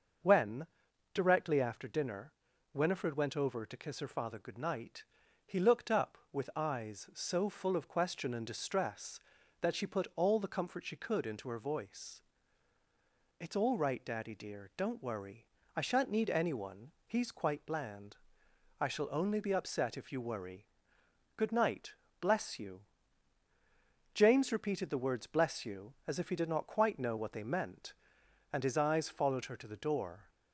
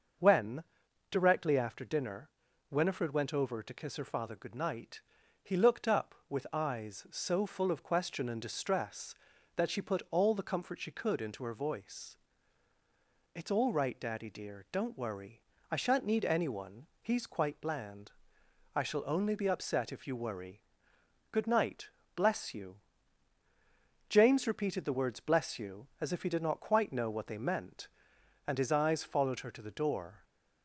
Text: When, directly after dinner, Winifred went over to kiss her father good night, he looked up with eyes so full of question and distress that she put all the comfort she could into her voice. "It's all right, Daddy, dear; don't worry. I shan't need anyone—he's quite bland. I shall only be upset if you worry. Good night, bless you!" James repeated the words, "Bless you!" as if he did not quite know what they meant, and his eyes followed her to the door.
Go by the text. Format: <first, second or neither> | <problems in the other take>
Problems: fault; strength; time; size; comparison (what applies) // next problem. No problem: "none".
neither | starts louder than the rest; noticeable; the same in both